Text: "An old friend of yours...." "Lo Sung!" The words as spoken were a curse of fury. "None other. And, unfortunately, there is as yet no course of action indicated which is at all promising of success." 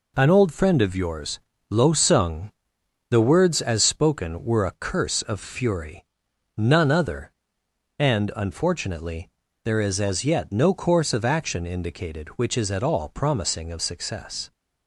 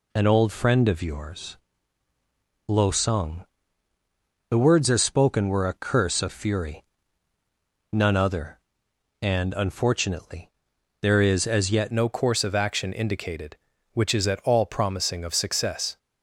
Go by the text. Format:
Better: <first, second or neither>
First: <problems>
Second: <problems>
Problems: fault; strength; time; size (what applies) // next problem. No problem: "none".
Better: first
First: none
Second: changes voice at "no"; from 11.9 s on; 4.0 s long